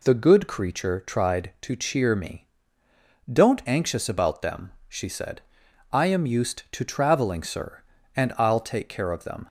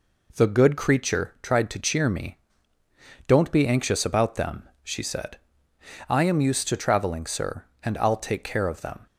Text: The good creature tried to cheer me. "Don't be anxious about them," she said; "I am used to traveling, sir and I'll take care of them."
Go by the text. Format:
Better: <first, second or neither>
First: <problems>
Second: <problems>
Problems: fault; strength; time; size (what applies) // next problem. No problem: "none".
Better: second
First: skips "be"; at 3.6 s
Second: none